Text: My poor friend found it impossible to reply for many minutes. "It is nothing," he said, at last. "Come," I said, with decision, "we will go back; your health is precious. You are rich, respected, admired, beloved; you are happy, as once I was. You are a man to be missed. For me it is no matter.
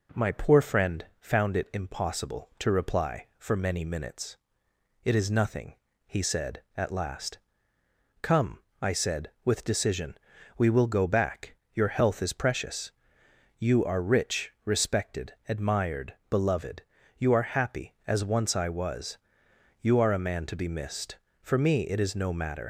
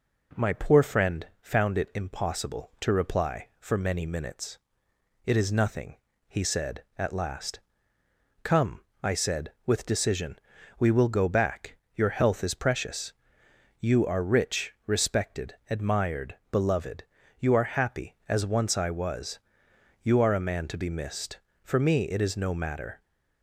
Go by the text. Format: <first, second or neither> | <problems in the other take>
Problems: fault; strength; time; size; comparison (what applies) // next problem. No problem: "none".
second | pauses between "friend" and "found"; slight; at 1.0 s; 0.16 s long; slight in the second // leaves "matter" unfinished; at 22.6 s; 110 ms